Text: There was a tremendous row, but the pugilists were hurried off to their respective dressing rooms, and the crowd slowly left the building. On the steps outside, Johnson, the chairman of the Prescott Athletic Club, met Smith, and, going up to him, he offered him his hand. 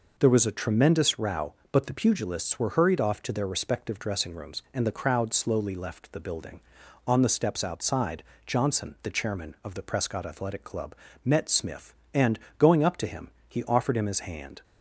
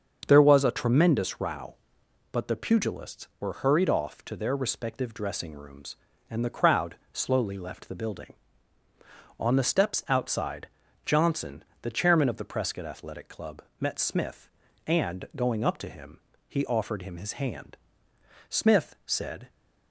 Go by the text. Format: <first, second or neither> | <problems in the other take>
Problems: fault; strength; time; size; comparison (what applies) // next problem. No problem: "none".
first | starts louder than the rest; until 1.2 s; 7 dB // pauses between "crowd" and "slowly"; slight; at 6.9 s; 0.16 s long // goes on to say "Smith said"; noticeable; from 18.4 s on; 1.0 s long